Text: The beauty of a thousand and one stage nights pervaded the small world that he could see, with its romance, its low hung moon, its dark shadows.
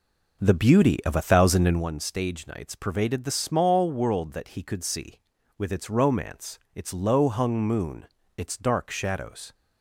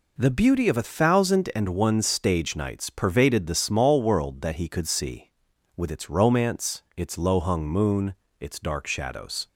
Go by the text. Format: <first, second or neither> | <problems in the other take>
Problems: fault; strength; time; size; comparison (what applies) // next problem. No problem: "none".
second | starts louder than the rest; noticeable; until 1.9 s; 5.5 dB